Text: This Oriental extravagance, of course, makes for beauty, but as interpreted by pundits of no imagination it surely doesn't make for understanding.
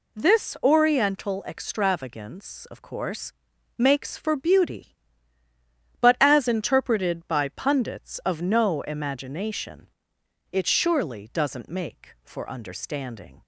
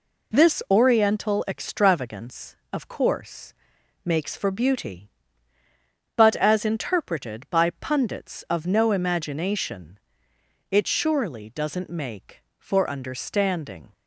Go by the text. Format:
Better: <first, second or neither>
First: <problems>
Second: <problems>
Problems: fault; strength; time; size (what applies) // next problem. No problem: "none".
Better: neither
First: pauses between "imagination" and "it"; noticeable; at 9.8 s; 0.64 s long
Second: pauses between "imagination" and "it"; noticeable; at 9.9 s; 0.72 s long